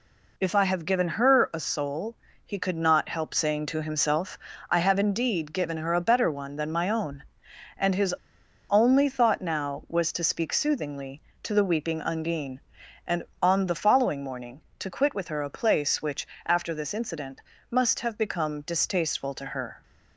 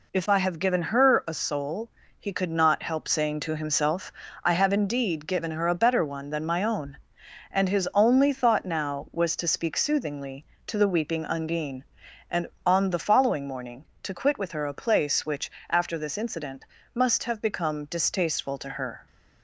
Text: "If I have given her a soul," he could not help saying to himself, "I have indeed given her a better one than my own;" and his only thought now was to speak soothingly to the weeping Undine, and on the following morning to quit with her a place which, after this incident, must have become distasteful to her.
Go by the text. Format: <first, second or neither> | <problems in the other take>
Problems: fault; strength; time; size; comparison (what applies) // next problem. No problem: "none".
second | pauses between "his" and "only"; noticeable; at 8.1 s; 0.56 s long